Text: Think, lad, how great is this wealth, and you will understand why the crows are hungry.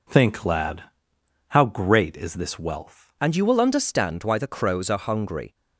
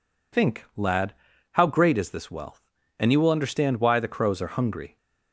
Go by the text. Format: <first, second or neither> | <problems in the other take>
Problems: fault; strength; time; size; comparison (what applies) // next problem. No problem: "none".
second | changes voice at "and"; from 3.2 s on; 2.3 s long